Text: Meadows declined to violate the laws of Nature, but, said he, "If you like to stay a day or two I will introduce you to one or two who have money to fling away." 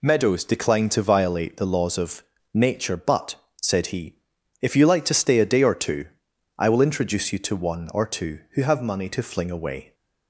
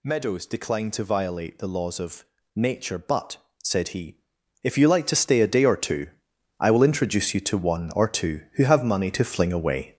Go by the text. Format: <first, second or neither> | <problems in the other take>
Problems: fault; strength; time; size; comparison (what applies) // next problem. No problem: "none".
first | gets louder; throughout; 6.5 dB // pauses between "of" and "Nature"; slight; at 2.2 s; 0.30 s long; slight in the first // pauses between "two" and "I"; noticeable; at 6.0 s; 0.50 s long; noticeable in the first